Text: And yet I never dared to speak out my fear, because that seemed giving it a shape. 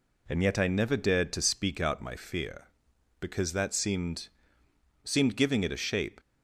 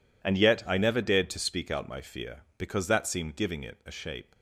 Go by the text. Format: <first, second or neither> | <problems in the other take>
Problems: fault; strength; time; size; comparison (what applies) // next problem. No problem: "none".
second | says "seemed" twice; at 5.0 s